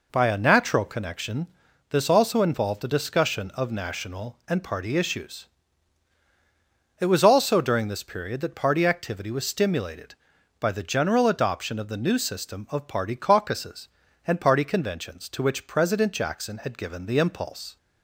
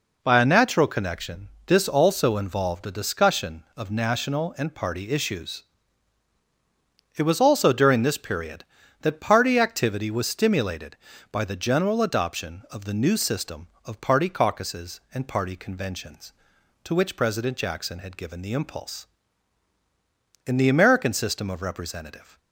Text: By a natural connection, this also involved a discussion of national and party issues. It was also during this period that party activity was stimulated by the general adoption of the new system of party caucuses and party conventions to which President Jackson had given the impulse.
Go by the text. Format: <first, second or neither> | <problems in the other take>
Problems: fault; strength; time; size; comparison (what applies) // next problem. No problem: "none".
first | goes on to say "In the American system of representative"; strong; from 20.4 s on; 1.9 s long